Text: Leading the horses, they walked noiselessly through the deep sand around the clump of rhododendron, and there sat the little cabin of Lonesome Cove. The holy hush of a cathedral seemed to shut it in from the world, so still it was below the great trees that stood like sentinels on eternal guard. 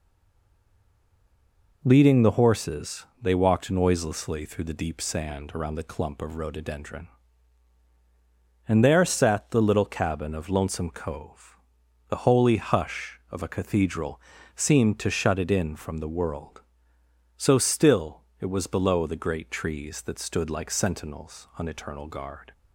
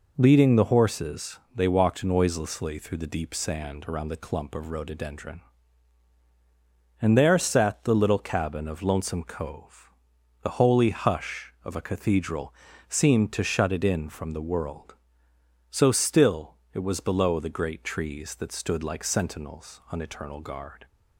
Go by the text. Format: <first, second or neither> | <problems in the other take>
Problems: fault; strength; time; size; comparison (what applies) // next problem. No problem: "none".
second | stays silent before the first word; noticeable; until 1.8 s; 1.8 s long // pauses between "cathedral" and "seemed"; slight; at 14.2 s; 0.34 s long; slight in the second // pauses between "still" and "it"; slight; at 18.2 s; 0.18 s long; slight in the second